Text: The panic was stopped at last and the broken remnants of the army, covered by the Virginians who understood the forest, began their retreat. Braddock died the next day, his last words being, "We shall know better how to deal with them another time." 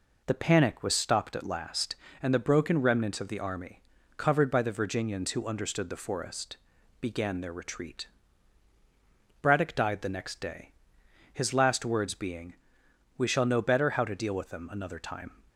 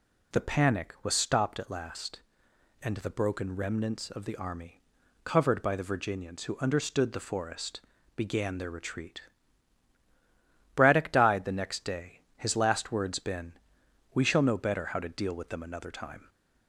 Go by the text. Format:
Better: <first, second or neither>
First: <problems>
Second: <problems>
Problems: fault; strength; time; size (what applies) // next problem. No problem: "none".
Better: first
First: none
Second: says "been" for "being"; at 13.1 s